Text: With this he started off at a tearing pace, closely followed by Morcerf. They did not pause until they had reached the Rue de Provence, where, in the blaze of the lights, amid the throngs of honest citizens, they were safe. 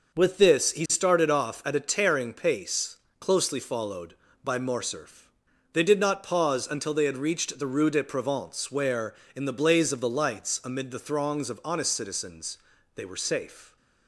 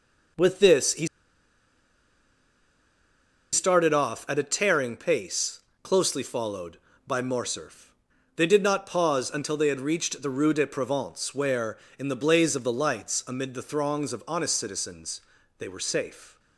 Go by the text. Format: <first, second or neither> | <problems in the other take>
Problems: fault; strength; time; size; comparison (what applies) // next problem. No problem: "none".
first | pauses between "he" and "started"; strong; at 1.0 s; 2.4 s long